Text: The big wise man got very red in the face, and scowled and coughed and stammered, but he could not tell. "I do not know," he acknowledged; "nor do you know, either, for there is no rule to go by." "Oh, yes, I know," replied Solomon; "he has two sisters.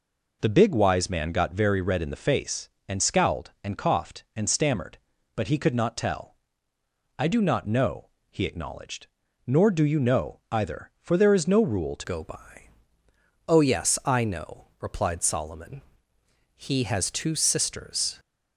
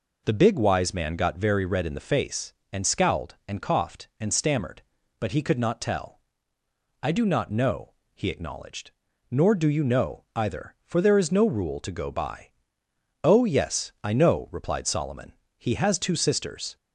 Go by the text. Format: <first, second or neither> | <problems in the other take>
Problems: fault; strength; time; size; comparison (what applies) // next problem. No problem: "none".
second | changes voice at "go"; from 12.0 s on; 6.1 s long